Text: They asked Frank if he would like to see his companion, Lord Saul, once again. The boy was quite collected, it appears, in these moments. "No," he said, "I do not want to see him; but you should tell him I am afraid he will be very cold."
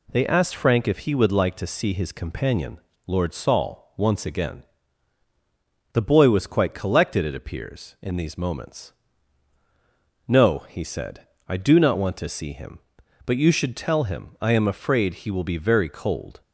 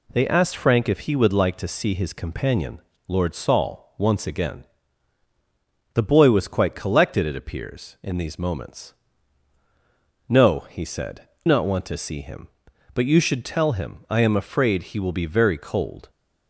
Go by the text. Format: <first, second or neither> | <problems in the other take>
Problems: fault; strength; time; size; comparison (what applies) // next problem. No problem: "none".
first | skips "I do"; at 11.3 s